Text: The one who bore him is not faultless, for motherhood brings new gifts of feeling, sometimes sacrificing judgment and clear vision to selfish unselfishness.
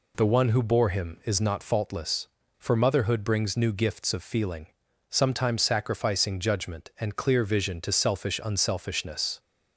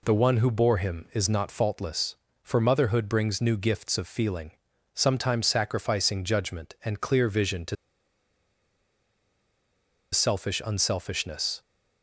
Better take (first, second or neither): first